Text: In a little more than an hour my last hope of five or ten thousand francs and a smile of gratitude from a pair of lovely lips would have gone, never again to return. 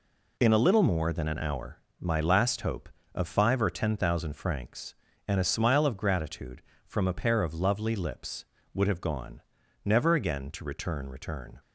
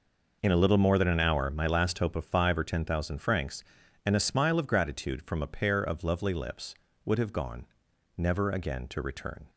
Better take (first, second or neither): second